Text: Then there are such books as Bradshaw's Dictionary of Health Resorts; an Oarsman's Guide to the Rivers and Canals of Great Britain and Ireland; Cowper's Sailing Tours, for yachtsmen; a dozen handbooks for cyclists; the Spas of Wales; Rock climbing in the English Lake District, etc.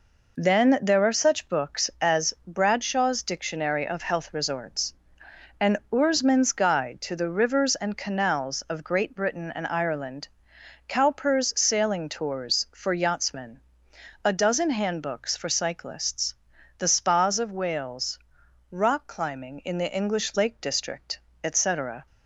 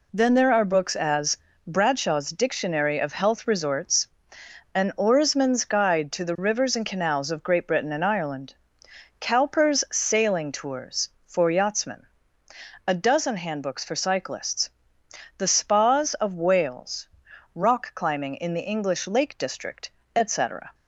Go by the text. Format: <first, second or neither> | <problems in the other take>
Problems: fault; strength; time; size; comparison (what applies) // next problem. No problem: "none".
first | skips "such"; at 0.6 s // pauses between "as" and "Bradshaw's"; slight; at 1.3 s; 0.30 s long